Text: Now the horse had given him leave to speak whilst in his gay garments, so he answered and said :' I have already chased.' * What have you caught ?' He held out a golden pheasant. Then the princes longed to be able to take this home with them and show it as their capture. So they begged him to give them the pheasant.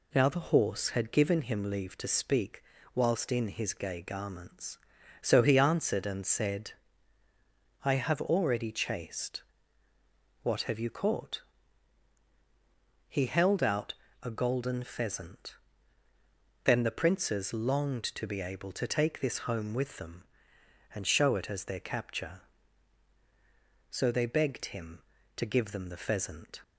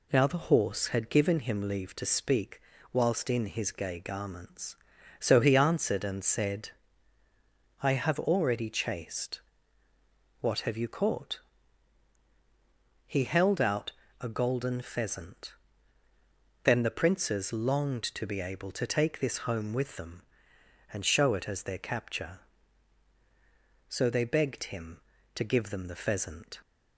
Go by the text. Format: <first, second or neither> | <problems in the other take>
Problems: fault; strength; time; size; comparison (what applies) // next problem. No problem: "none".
neither | pauses between "speak" and "whilst"; slight; the same in both // pauses between "out" and "a"; slight; the same in both